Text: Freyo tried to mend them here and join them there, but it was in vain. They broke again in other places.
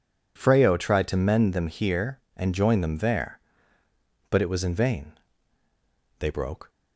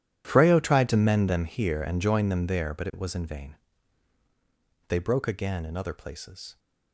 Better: second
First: stops before "again in other places"; at 6.6 s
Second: none

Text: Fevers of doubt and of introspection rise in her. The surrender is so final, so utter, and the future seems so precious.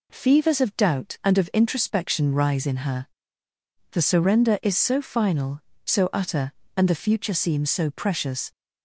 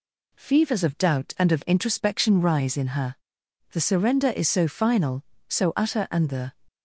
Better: first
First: none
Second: stops before "future seems so precious"; at 6.6 s

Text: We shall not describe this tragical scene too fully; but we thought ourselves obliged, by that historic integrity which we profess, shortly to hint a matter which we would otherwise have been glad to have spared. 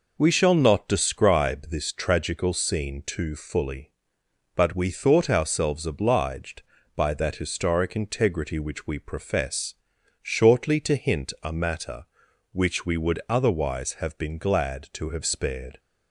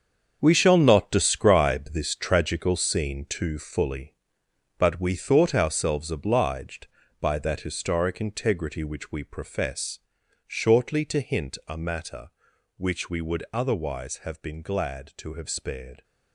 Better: first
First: none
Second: gets quieter; strong; throughout; 11.5 dB

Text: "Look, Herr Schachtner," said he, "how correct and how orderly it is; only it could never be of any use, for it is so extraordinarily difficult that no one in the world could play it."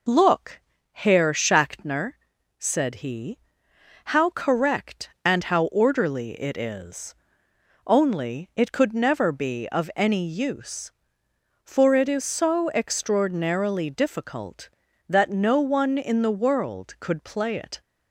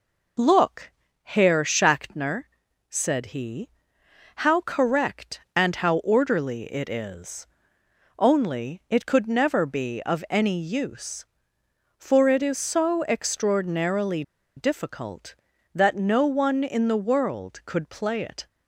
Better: first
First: none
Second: pauses between "extraordinarily" and "difficult"; slight; at 14.2 s; 0.34 s long

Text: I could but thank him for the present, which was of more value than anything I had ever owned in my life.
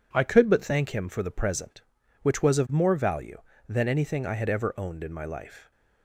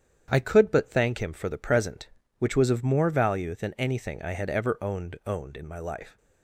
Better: first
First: none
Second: starts louder than the rest; strong; until 1.3 s; 8.5 dB // says "owned" twice; at 5.2 s

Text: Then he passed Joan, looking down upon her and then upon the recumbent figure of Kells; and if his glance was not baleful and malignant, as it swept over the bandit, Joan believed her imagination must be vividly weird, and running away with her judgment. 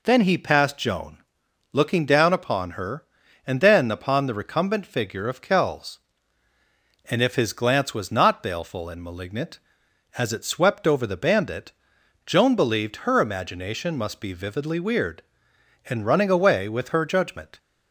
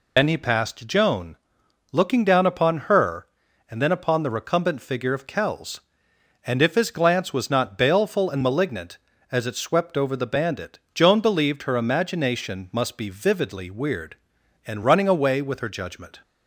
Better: first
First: none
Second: loses the start of "Then"; at 0.1 s; 90 ms

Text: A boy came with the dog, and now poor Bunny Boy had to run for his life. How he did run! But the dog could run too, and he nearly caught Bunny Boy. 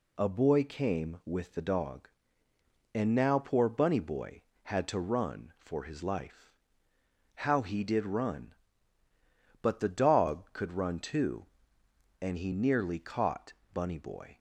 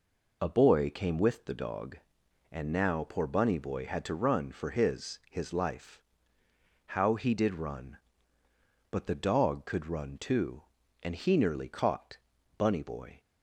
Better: first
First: pauses between "caught" and "Bunny"; slight; at 13.5 s; 0.20 s long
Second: says "his" twice; at 5.2 s // pauses between "caught" and "Bunny"; at 12.1 s; 0.40 s long

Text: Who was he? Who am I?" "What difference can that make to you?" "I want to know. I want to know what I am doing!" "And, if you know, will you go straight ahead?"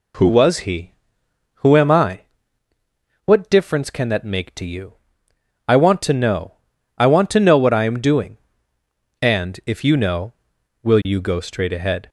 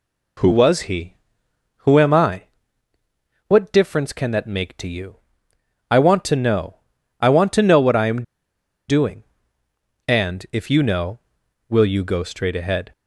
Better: first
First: none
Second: pauses between "am" and "doing"; noticeable; at 8.2 s; 0.66 s long

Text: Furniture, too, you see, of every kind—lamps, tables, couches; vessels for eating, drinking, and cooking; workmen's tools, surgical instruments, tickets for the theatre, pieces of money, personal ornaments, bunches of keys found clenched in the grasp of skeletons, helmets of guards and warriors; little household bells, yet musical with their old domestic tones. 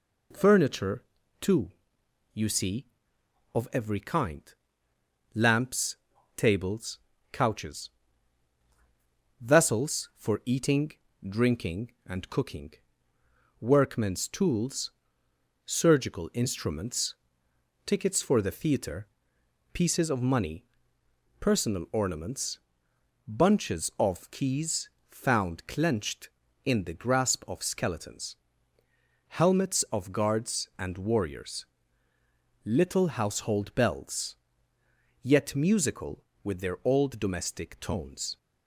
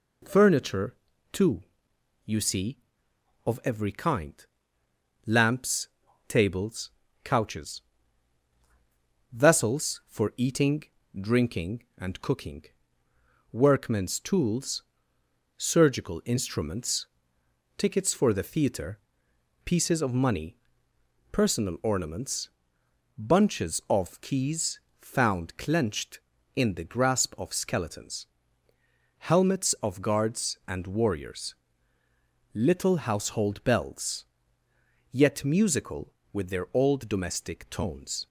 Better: neither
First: pauses between "keys" and "found"; slight; at 24.8 s; 0.20 s long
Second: pauses between "keys" and "found"; slight; at 24.7 s; 0.20 s long

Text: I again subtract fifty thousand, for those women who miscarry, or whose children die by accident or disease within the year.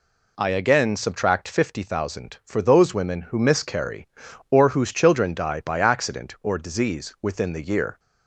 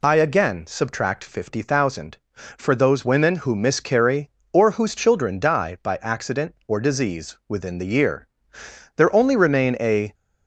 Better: first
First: none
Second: goes on to say "There only remain a"; noticeable; from 8.9 s on; 1.1 s long

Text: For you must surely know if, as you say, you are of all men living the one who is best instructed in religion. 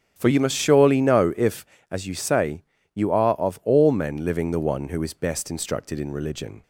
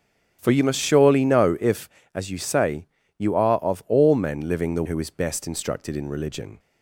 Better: first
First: starts louder than the rest; strong; until 1.1 s; 8.5 dB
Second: starts louder than the rest; strong; until 1.4 s; 8 dB // skips "one"; at 4.8 s

